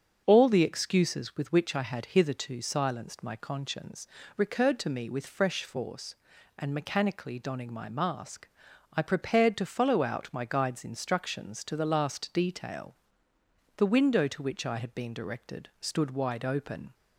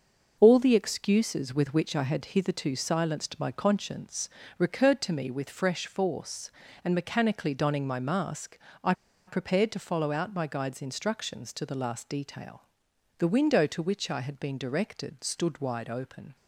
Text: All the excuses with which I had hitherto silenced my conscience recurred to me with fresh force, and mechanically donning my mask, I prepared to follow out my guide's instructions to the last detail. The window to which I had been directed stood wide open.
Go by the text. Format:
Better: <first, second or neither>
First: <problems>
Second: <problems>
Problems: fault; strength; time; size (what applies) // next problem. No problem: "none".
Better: first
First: starts louder than the rest; until 1.2 s; 7 dB // pauses between "conscience" and "recurred"; slight; at 4.0 s; 0.29 s long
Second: starts louder than the rest; until 1.4 s; 6 dB // pauses between "conscience" and "recurred"; slight; at 4.2 s; 0.28 s long // pauses between "I" and "prepared"; slight; at 8.9 s; 0.33 s long